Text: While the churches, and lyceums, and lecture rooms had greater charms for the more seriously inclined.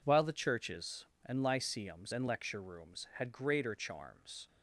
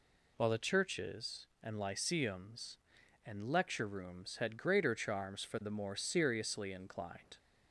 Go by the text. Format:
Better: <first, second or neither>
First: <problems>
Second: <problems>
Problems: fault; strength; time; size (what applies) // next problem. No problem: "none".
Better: second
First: stops before "for the more seriously inclined"; at 4.4 s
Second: none